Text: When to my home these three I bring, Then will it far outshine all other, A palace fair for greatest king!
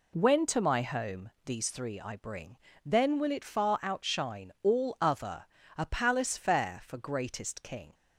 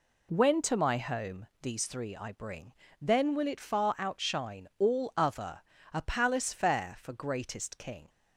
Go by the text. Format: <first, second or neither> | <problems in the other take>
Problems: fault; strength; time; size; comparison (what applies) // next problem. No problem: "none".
neither | none